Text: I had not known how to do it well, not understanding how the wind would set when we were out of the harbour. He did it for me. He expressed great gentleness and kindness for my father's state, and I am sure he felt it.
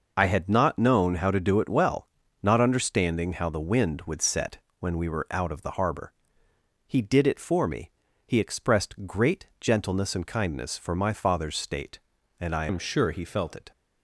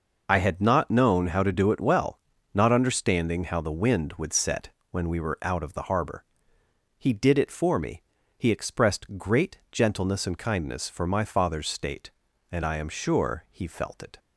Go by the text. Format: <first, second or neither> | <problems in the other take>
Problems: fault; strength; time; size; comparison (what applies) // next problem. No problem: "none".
second | pauses between "set" and "when"; slight; at 4.5 s; 0.20 s long; slight in the second // changes voice from "am" to "felt"; from 12.6 to 13.5 s; 0.9 s long